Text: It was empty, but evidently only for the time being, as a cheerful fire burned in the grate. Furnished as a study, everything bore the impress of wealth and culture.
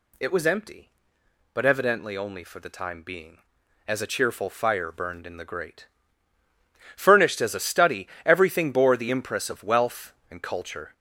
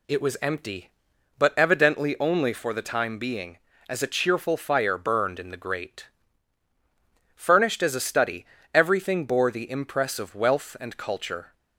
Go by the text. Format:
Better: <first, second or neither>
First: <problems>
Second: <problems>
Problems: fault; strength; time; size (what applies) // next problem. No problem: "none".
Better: second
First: gets louder; noticeable; throughout; 5 dB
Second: none